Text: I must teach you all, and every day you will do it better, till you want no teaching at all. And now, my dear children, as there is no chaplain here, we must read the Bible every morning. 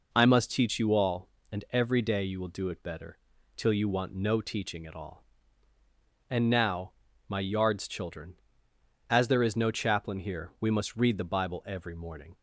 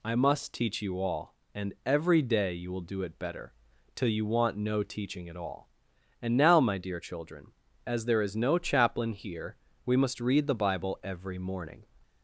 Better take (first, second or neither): second